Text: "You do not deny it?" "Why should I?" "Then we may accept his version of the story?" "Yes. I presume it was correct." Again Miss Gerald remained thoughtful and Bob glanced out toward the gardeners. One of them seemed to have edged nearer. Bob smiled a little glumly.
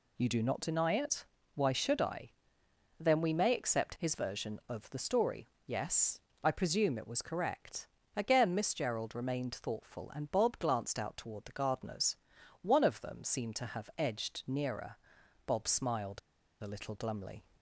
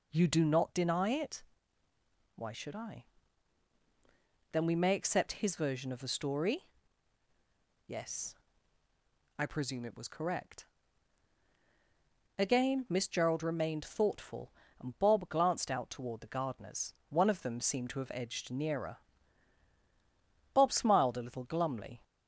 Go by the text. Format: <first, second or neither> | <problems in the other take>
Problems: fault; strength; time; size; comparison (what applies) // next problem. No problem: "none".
second | pauses between "smiled" and "a"; at 16.1 s; 0.42 s long